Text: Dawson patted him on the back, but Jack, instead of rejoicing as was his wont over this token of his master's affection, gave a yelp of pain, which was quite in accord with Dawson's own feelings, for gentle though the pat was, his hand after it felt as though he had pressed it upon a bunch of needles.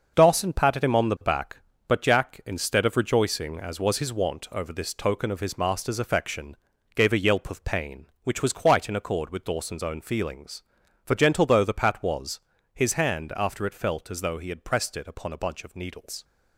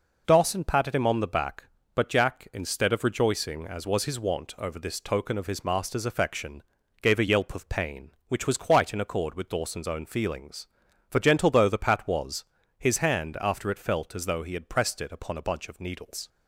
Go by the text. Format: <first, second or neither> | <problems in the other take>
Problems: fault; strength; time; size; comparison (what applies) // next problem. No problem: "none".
second | gets quieter; strong; throughout; 8 dB